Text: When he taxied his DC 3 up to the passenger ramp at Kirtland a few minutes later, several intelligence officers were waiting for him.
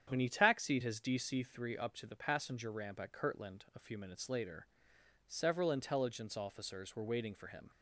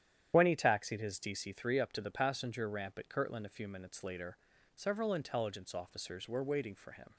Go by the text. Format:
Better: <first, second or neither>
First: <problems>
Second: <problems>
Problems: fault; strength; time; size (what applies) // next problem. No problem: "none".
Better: first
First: starts louder than the rest; strong; until 1.1 s; 8.5 dB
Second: loses the start of "When"; at 0.3 s; 25 ms // starts louder than the rest; strong; until 1.3 s; 10 dB